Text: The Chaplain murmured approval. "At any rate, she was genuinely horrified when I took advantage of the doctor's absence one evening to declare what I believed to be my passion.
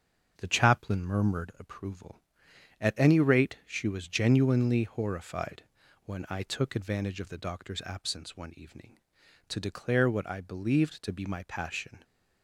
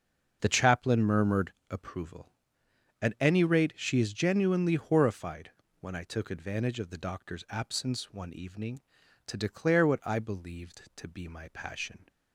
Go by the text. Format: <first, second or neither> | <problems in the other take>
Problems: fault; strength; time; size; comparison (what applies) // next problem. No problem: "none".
first | starts louder than the rest; until 1.4 s; 6.5 dB; also in the first // pauses between "murmured" and "approval"; slight; at 1.5 s; 0.18 s long // says "is" for "was"; at 3.9 s // pauses between "horrified" and "when"; slight; at 5.4 s; 0.32 s long; also in the first